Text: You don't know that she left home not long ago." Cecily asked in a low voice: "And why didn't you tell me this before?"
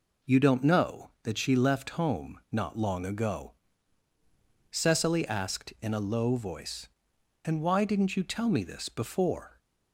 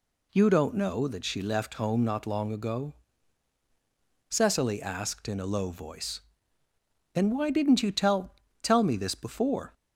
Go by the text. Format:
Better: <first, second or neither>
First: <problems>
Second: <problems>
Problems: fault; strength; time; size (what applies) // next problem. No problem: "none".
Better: first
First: none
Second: says "tell" twice; at 8.6 s